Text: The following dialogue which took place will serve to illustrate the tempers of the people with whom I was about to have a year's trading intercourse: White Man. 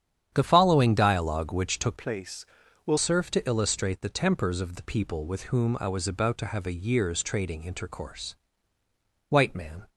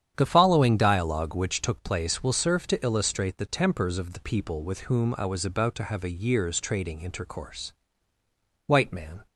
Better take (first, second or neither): second